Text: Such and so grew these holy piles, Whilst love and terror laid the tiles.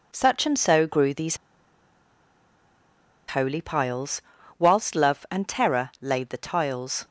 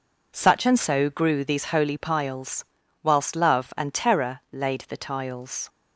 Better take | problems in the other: second | pauses between "these" and "holy"; strong; at 1.3 s; 1.9 s long

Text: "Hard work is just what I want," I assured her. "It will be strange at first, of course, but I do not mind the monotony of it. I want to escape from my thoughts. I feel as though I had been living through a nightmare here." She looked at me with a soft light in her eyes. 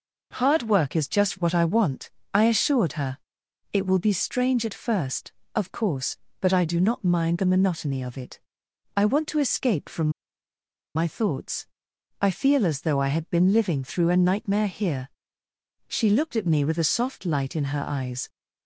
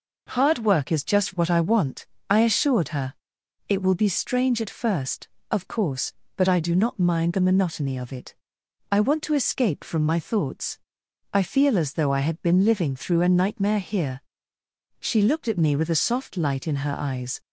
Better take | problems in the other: second | pauses between "from" and "my"; noticeable; at 10.0 s; 0.85 s long

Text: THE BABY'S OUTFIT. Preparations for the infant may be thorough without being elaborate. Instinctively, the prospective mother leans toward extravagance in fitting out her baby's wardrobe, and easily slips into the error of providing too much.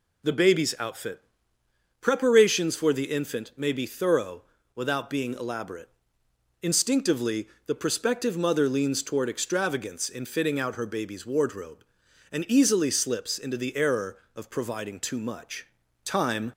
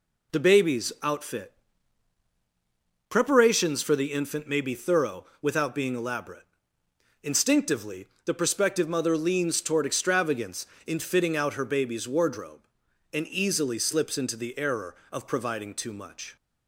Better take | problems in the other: second | pauses between "thorough" and "without"; slight; at 4.4 s; 0.32 s long; slight in the second // goes on to say "Time"; slight; from 16.0 s on; 0.48 s long

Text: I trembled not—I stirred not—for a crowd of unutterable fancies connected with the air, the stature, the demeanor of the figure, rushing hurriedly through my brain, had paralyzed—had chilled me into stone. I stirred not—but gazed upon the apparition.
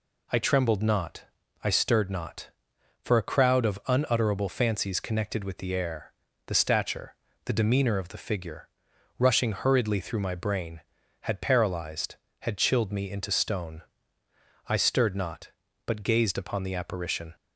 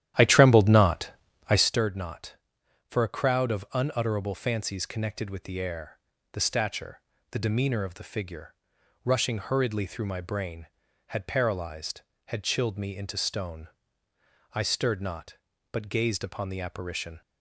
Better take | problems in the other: first | starts louder than the rest; strong; until 1.8 s; 12 dB

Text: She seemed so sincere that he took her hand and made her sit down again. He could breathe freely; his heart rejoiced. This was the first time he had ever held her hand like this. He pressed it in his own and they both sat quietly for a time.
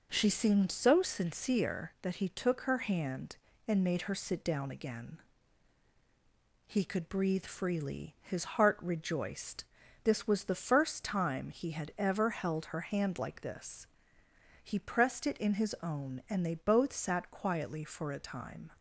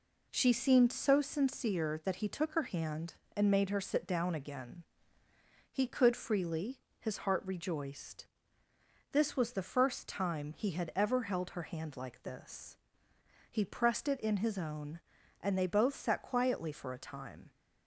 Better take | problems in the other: first | skips "breathe"; at 6.1 s

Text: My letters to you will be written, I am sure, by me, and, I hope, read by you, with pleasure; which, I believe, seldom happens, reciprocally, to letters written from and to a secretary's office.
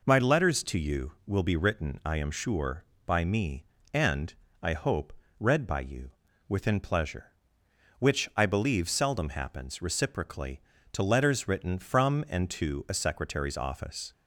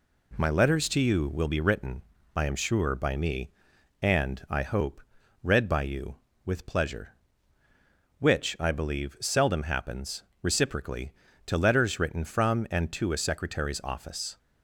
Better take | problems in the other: second | says "within" for "with"; at 6.4 s

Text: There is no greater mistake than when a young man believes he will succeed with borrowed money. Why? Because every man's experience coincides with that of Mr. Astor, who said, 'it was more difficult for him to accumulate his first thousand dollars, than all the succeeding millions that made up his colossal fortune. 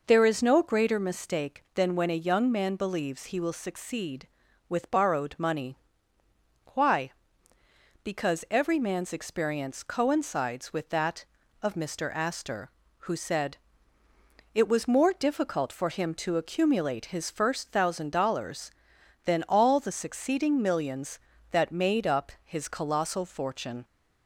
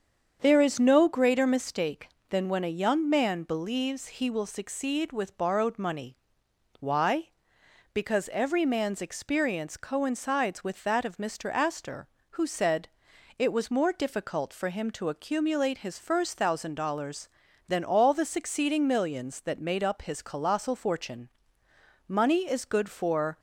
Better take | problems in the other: first | starts louder than the rest; strong; until 1.4 s; 7.5 dB // goes on to say "Money is good for"; noticeable; from 22.1 s on; 1.2 s long

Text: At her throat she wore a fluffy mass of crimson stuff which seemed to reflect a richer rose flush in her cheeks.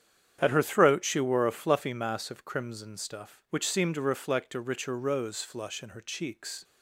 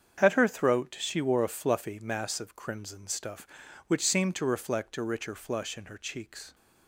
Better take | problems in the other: first | starts louder than the rest; strong; until 1.2 s; 7.5 dB; strong in the first // skips "rose"; at 5.3 s

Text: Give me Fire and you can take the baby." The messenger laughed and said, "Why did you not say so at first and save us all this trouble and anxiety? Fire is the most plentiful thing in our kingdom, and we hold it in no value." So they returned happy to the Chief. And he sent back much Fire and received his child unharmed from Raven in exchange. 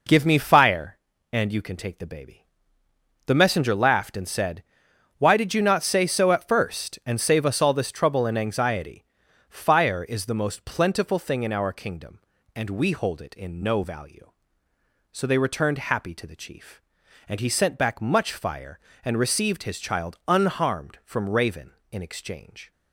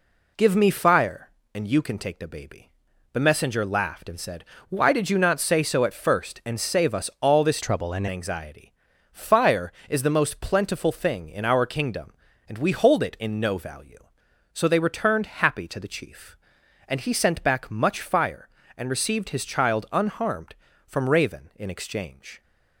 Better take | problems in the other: first | changes voice from "trouble" to "and"; from 7.6 to 8.0 s; 0.4 s long

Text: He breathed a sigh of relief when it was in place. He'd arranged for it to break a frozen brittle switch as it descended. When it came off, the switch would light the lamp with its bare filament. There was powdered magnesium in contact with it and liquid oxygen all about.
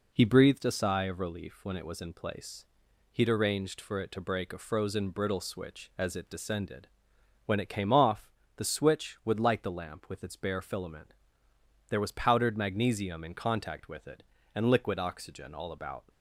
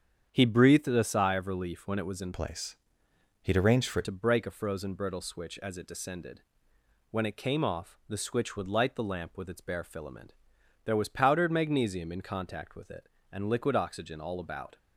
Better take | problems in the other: first | starts louder than the rest; strong; until 1.3 s; 8 dB // changes voice from "place" to "it"; from 2.3 to 4.0 s; 1.7 s long

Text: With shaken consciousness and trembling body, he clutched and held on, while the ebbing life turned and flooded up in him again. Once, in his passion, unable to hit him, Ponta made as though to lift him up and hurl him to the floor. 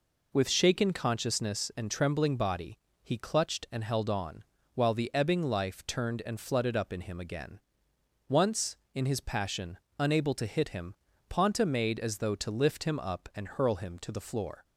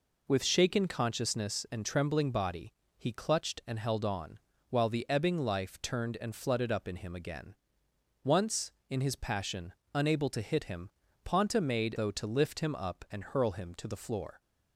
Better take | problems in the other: first | skips "as"; at 11.9 s

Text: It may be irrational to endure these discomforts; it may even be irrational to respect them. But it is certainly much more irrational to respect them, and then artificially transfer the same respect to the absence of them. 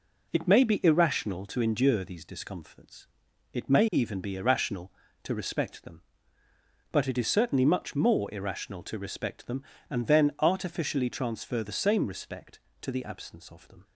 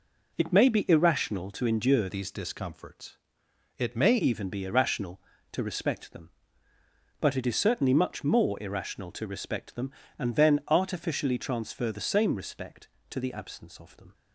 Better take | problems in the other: first | changes voice from "these" to "may"; from 2.0 to 4.1 s; 2.1 s long

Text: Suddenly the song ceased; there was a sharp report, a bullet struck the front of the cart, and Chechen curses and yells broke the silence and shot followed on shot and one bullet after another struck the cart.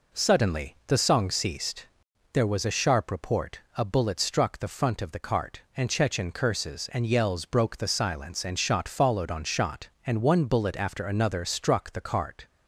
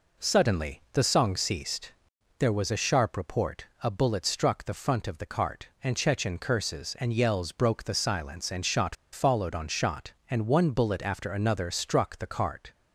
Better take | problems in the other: first | pauses between "shot" and "followed"; slight; at 8.9 s; 0.17 s long

